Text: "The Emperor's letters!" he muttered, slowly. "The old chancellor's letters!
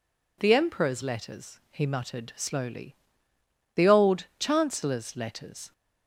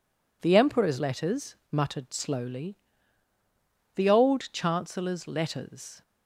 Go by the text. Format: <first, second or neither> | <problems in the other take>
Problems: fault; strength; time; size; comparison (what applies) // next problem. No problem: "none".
first | skips "he"; at 1.6 s